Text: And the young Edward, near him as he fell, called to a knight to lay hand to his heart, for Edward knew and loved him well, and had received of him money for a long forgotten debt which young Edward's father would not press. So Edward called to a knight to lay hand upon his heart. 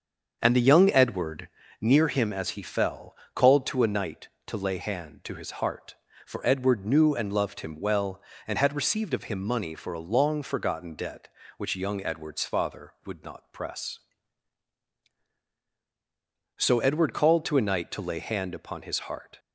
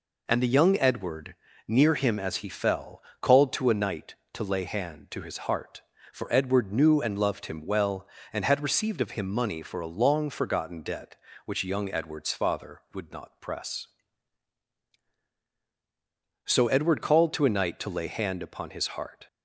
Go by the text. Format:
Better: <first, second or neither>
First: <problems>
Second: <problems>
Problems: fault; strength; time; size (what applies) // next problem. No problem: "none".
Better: second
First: starts louder than the rest; until 2.0 s; 7 dB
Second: none